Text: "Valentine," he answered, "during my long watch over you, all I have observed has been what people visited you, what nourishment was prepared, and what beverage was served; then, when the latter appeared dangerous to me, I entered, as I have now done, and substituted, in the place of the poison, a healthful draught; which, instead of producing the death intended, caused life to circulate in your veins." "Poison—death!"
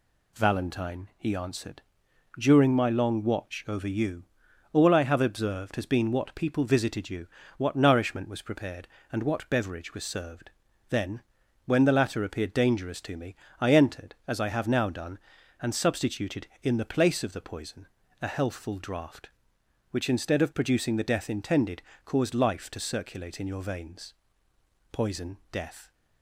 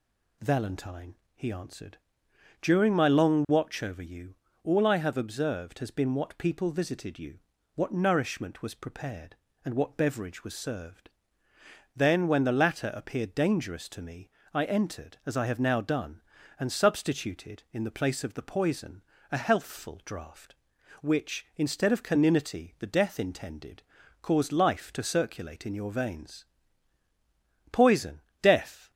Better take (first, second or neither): first